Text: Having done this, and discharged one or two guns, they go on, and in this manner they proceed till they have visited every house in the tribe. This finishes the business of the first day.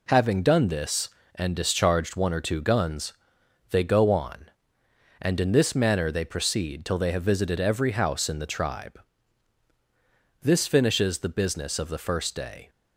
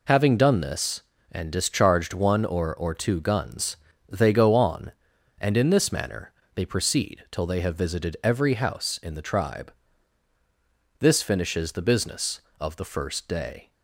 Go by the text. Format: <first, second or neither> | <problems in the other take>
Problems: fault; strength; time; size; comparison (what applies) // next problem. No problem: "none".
first | says "or" twice; at 2.7 s // pauses between "manner" and "they"; slight; at 6.3 s; 0.22 s long